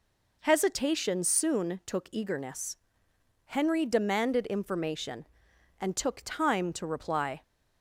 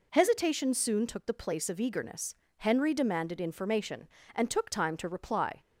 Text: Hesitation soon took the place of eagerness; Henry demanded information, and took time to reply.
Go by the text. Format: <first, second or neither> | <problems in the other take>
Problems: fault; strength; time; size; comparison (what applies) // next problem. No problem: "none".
second | skips "the place of"; at 2.0 s